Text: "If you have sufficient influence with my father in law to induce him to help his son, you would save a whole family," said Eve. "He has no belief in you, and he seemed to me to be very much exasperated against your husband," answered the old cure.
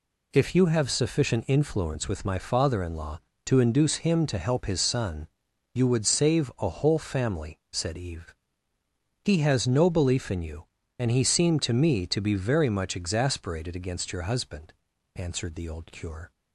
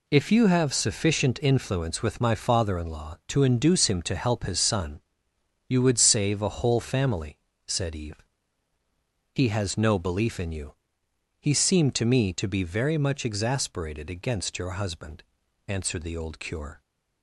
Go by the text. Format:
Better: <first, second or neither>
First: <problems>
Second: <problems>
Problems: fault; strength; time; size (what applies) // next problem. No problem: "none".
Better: first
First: none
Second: skips "and"; at 11.0 s